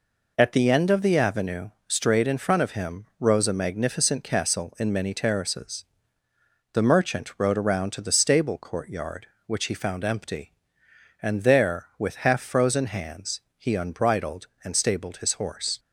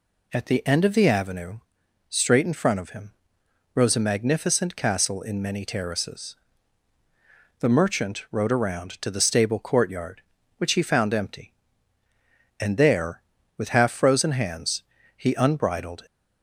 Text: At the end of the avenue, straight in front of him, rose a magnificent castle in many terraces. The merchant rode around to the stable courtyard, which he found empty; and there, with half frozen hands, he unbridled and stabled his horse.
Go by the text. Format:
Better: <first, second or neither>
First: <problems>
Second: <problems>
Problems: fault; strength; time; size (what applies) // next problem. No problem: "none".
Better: first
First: none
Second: stops before "and stabled his horse"; at 16.0 s